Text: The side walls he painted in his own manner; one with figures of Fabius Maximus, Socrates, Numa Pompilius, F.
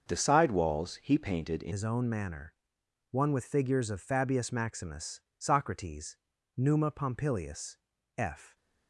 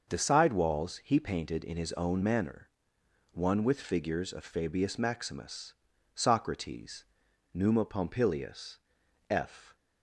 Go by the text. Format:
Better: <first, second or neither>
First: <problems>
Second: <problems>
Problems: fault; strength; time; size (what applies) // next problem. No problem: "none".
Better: second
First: starts louder than the rest; until 1.1 s; 6.5 dB // changes voice at "his"; from 1.7 s on; 6.8 s long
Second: starts louder than the rest; until 1.1 s; 6 dB